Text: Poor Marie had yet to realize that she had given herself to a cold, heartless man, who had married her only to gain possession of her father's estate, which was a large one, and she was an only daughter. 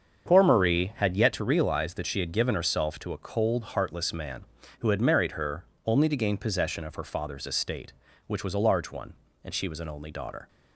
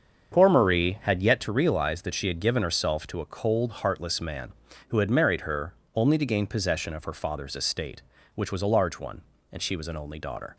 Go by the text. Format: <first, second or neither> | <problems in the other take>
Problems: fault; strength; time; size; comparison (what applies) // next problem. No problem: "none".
neither | starts louder than the rest; strong; the same in both // pauses between "her" and "only"; slight; the same in both